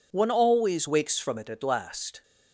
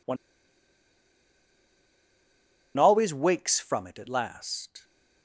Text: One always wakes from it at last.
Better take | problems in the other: first | pauses between "One" and "always"; strong; at 0.1 s; 2.6 s long

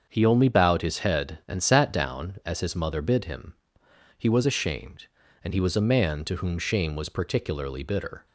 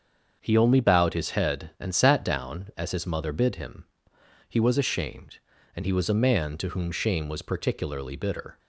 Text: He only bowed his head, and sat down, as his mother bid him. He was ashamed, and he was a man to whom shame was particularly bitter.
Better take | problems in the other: neither | starts louder than the rest; the same in both

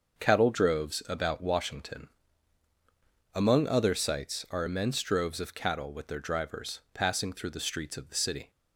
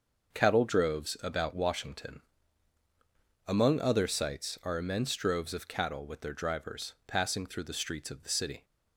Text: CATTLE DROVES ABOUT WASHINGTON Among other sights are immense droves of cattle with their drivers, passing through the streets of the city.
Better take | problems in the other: neither | starts louder than the rest; the same in both // pauses between "WASHINGTON" and "Among"; strong; the same in both

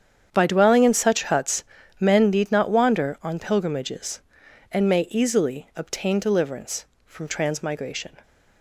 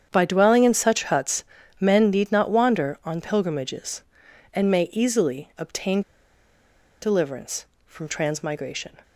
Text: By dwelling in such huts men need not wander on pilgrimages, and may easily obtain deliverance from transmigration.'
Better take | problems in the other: first | starts louder than the rest; strong; until 1.1 s; 8 dB; strong in the first // pauses between "huts" and "men"; slight; at 1.4 s; 0.34 s long; slight in the first // pauses between "obtain" and "deliverance"; at 6.0 s; 1.0 s long

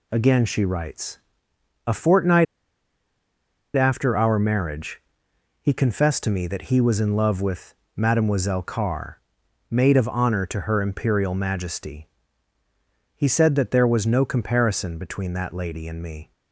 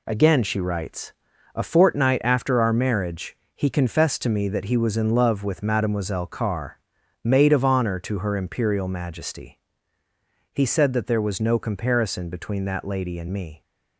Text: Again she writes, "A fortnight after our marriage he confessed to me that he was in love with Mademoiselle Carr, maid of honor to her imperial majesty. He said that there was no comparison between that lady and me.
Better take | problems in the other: second | pauses between "fortnight" and "after"; strong; at 2.4 s; 1.3 s long // pauses between "marriage" and "he"; noticeable; at 4.9 s; 0.62 s long; slight in the second // pauses between "with" and "Mademoiselle"; slight; at 7.7 s; 0.22 s long

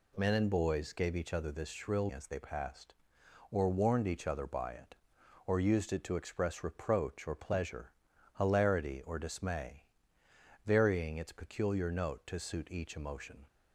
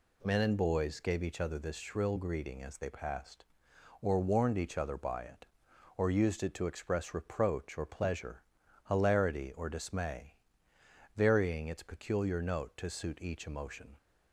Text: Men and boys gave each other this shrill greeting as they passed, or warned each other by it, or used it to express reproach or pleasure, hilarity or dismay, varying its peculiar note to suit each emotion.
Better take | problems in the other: second | skips "greeting"; at 2.1 s

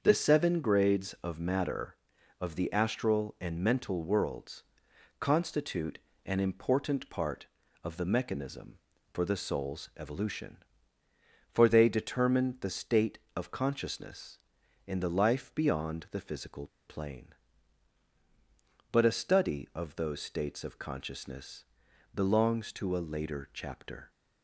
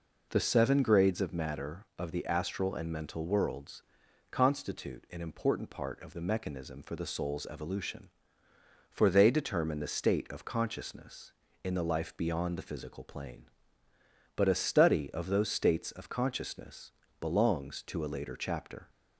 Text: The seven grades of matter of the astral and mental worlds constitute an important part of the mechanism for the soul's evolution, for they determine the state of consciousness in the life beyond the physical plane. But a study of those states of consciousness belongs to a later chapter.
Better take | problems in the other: second | starts louder than the rest; until 1.0 s; 6.5 dB // pauses between "worlds" and "constitute"; noticeable; at 4.6 s; 0.56 s long; noticeable in the second // pauses between "constitute" and "an"; slight; at 5.9 s; 0.26 s long // pauses between "physical" and "plane"; slight; at 16.6 s; 0.20 s long // pauses between "consciousness" and "belongs"; noticeable; at 21.6 s; 0.48 s long; slight in the second

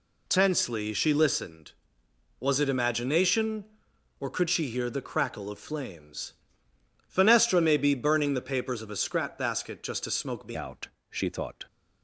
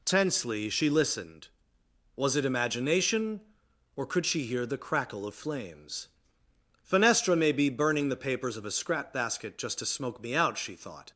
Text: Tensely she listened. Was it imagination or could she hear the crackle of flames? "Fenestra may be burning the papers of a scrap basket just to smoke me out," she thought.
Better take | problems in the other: second | changes voice at "out"; from 10.5 s on; 1.1 s long

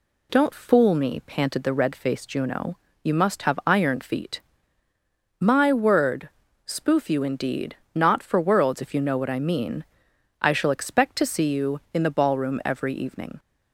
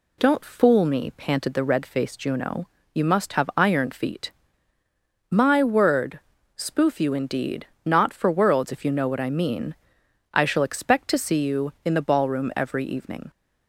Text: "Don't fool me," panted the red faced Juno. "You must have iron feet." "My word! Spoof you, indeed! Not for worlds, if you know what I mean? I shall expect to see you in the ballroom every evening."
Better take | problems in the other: neither | none

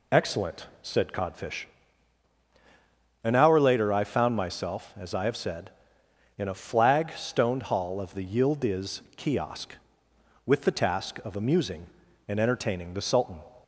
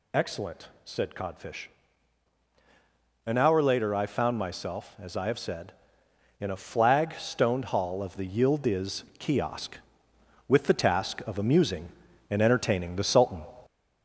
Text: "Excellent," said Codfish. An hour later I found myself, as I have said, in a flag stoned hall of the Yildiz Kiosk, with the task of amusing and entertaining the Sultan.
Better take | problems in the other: first | gets louder; noticeable; throughout; 4.5 dB

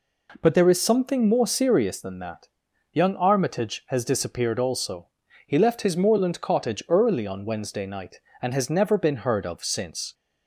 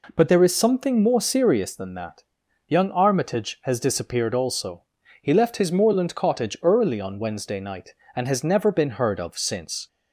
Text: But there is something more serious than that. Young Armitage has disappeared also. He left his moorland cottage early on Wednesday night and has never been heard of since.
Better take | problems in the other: neither | none

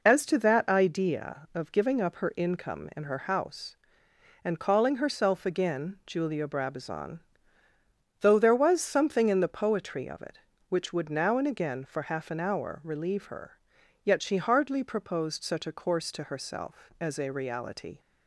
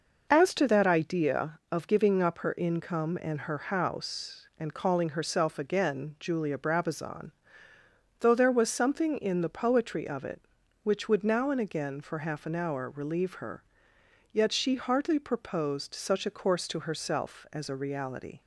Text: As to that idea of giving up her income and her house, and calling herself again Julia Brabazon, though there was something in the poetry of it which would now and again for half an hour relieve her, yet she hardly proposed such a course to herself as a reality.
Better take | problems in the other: neither | none

